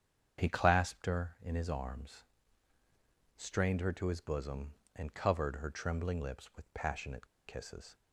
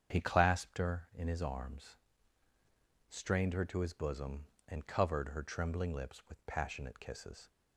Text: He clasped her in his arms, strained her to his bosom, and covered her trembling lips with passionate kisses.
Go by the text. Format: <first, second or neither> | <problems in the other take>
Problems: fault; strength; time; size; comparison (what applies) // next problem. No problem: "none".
second | starts louder than the rest; strong; until 1.4 s; 8 dB; strong in the second // pauses between "passionate" and "kisses"; slight; at 7.2 s; 0.20 s long